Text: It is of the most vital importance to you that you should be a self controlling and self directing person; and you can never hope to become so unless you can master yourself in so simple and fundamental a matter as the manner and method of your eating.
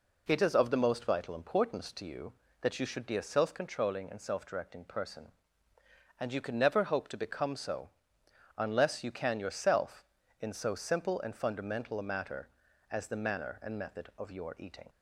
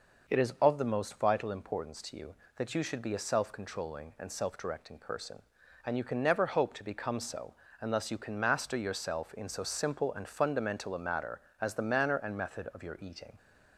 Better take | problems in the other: second | pauses between "so" and "unless"; noticeable; at 7.9 s; 0.66 s long; slight in the second // skips "master"; at 9.3 s

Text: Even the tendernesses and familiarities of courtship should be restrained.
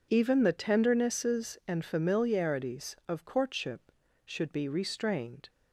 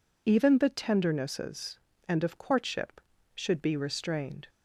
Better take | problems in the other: first | skips "familiarities"; at 2.2 s

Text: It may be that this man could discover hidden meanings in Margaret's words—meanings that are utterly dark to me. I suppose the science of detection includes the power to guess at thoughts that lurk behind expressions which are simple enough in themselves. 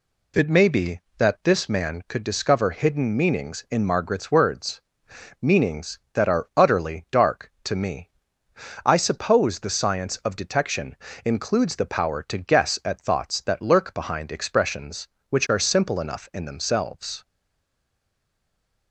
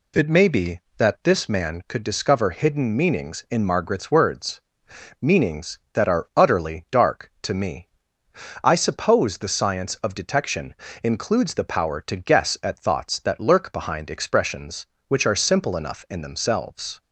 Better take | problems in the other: second | pauses between "detection" and "includes"; slight; at 10.9 s; 0.26 s long; slight in the second // stays silent after the last word; noticeable; from 17.2 s on; 1.7 s long

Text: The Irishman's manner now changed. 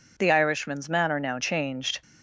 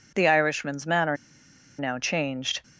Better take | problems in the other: first | pauses between "manner" and "now"; noticeable; at 1.1 s; 0.62 s long

